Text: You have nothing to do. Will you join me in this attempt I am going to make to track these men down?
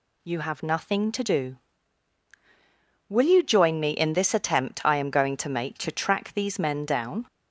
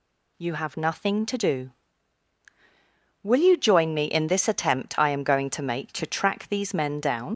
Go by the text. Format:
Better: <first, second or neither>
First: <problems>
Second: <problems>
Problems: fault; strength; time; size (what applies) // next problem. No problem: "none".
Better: first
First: none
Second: leaves "down" unfinished; at 7.3 s; 65 ms